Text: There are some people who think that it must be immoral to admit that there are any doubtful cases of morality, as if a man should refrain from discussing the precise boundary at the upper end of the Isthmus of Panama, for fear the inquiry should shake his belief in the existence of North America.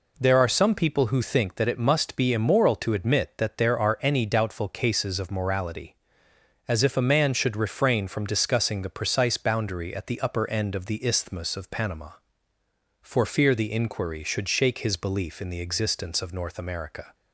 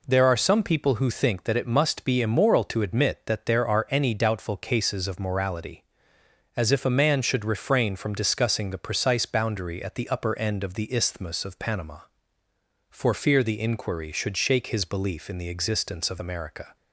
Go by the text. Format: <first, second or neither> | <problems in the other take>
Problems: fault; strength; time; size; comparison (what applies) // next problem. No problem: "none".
first | skips "North"; at 16.2 s